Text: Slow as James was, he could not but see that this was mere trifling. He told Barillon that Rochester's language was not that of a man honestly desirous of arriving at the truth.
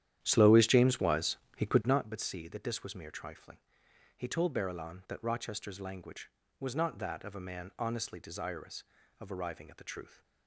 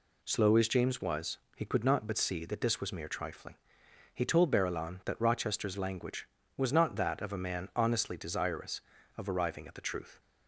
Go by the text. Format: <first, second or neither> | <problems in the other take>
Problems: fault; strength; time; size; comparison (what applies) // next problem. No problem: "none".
second | starts louder than the rest; strong; until 2.1 s; 11 dB